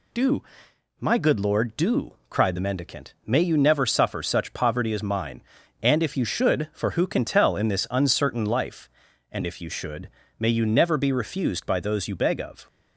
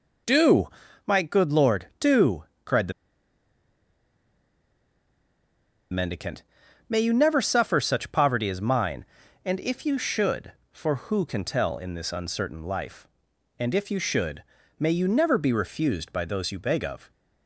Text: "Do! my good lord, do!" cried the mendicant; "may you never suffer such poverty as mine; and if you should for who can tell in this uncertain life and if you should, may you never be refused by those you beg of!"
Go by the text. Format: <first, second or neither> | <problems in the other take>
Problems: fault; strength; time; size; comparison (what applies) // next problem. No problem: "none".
first | pauses between "the" and "mendicant"; strong; at 2.9 s; 2.9 s long